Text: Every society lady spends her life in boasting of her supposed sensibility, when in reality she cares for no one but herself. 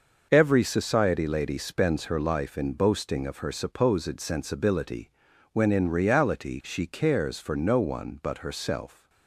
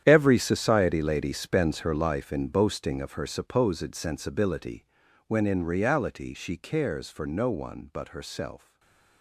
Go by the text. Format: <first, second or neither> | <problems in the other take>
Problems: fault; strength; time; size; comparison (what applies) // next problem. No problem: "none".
first | gets quieter; strong; throughout; 15 dB // stays silent after the last word; slight; from 8.5 s on; 0.7 s long